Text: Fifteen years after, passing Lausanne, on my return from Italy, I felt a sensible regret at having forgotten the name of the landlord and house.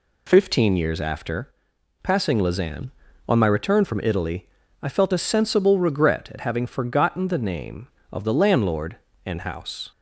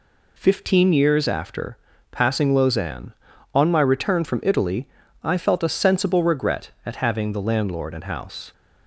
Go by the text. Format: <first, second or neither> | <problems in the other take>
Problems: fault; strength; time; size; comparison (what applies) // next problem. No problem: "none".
first | skips "forgotten the name of"; at 7.3 s